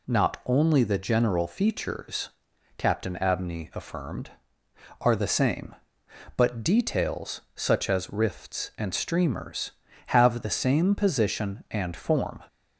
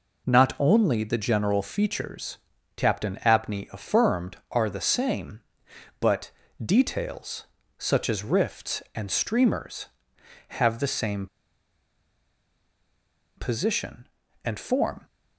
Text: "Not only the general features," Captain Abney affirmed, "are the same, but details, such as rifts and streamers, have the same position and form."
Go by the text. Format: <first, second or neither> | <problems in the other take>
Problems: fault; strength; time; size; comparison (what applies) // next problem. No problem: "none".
first | pauses between "but" and "details"; slight; at 6.3 s; 0.34 s long // pauses between "same" and "position"; strong; at 11.2 s; 2.1 s long